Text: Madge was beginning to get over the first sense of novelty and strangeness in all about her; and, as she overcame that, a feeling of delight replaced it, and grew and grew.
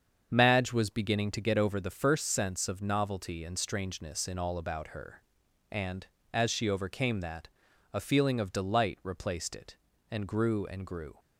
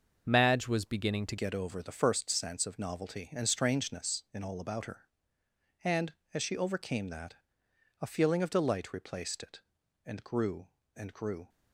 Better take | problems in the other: first | starts louder than the rest; until 1.2 s; 6 dB; strong in the first // changes voice at "get"; from 1.3 s on; 10.1 s long

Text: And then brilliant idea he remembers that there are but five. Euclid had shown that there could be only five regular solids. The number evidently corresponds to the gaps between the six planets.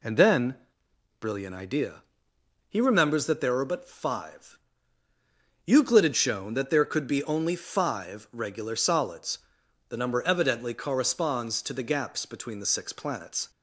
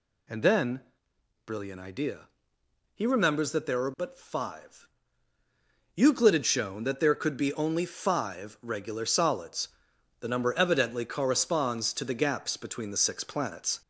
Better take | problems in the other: first | gets louder; slight; throughout; 3 dB // pauses between "then" and "brilliant"; noticeable; at 0.8 s; 0.64 s long; noticeable in the first // pauses between "idea" and "he"; noticeable; at 2.2 s; 0.66 s long; noticeable in the first

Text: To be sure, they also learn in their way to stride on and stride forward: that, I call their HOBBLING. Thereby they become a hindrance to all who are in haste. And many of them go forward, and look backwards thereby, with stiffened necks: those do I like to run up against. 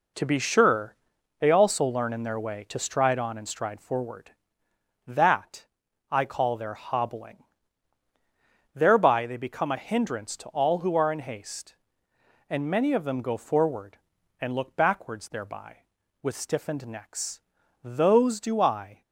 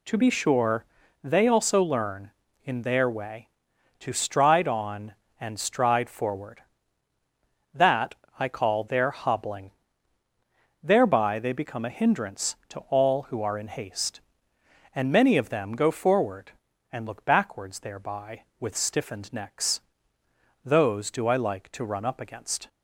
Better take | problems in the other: second | stops before "like to run up against"; at 19.0 s

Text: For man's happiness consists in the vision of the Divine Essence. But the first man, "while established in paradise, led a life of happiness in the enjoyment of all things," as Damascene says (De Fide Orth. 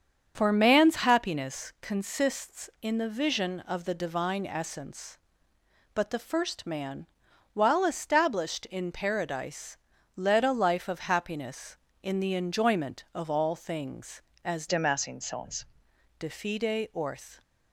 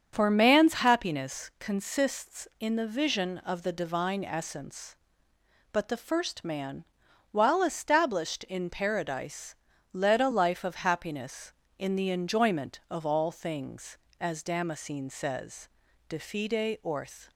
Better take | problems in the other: second | starts louder than the rest; strong; until 1.3 s; 7.5 dB; strong in the second // changes voice from "Damascene" to "says"; from 14.6 to 15.6 s; 1.0 s long

